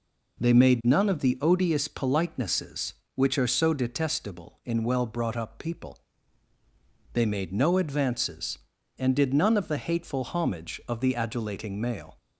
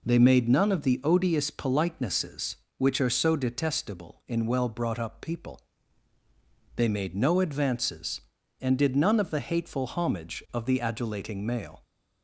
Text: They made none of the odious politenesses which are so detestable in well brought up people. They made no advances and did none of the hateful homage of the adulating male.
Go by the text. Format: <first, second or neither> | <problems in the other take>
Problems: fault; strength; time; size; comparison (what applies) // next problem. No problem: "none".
neither | none